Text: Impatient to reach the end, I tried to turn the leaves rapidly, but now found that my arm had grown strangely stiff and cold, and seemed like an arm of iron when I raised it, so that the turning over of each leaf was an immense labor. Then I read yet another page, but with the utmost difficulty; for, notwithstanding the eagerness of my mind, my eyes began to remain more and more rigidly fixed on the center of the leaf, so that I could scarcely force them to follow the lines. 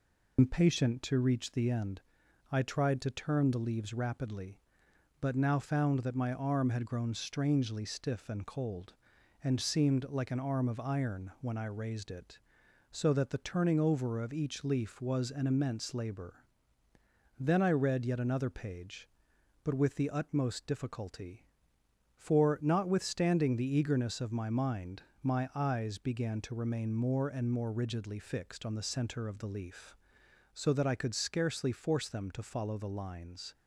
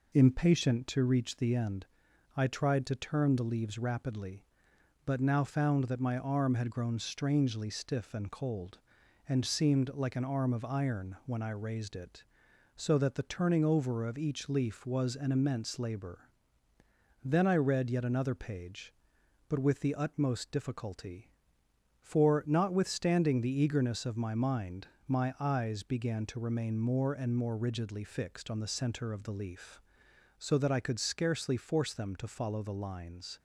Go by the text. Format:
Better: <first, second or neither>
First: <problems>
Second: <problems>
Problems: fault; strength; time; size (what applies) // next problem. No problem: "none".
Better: second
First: loses the start of "Impatient"; at 0.3 s; 95 ms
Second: none